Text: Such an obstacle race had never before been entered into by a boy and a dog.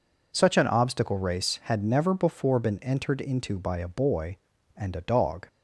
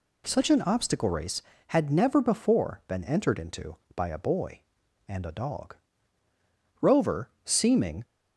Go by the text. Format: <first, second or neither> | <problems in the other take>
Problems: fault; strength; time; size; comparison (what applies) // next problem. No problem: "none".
first | goes on to say "Rover seeming"; noticeable; from 6.8 s on; 1.2 s long